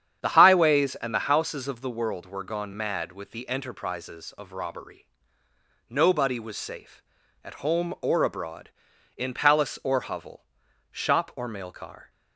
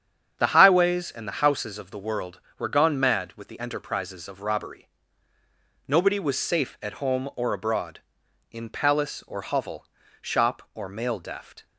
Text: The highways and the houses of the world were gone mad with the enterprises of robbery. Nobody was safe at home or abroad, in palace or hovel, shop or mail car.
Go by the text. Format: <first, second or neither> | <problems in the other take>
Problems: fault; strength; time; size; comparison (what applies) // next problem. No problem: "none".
first | starts louder than the rest; strong; until 1.3 s; 8 dB; strong in the first // says "deft" for "car"; at 11.1 s